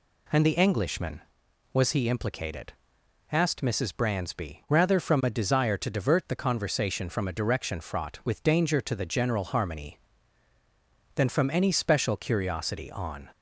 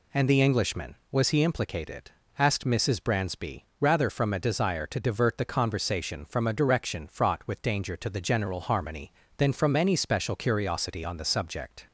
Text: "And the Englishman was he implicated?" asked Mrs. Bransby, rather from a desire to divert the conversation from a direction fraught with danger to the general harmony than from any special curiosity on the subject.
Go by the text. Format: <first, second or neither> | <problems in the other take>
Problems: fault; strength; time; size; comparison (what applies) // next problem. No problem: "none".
second | stops before "the subject"; at 13.3 s